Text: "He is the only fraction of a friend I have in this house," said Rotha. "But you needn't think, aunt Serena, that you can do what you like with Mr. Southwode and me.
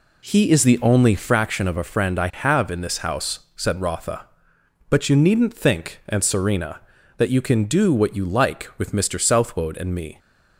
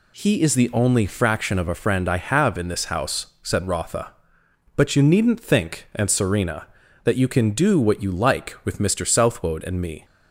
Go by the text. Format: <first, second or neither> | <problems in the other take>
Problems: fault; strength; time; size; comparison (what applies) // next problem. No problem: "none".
second | starts louder than the rest; slight; until 1.5 s; 2.5 dB